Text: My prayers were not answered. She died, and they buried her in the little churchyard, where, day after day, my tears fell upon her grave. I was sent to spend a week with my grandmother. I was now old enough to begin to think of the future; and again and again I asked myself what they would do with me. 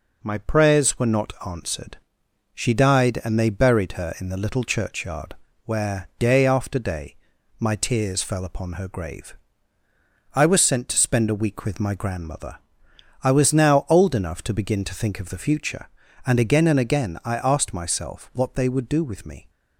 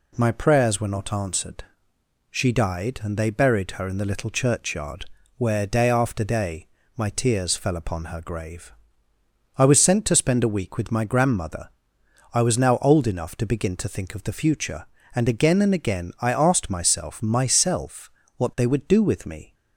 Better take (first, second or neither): first